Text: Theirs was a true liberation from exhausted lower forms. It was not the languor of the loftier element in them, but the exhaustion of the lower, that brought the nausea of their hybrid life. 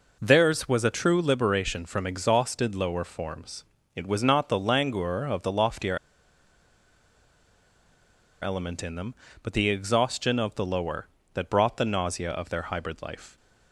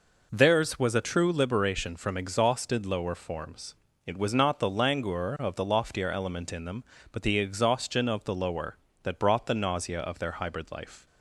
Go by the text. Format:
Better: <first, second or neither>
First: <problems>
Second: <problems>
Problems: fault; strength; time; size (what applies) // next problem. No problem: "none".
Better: second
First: pauses between "loftier" and "element"; strong; at 5.9 s; 2.4 s long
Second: none